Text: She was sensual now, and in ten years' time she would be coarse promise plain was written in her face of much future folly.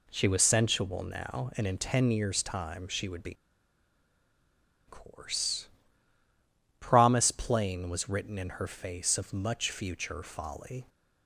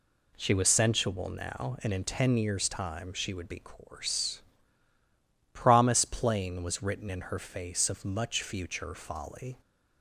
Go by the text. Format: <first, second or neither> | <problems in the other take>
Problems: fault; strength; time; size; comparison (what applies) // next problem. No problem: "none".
second | pauses between "be" and "coarse"; strong; at 3.3 s; 1.5 s long // pauses between "coarse" and "promise"; at 5.6 s; 1.1 s long; also in the second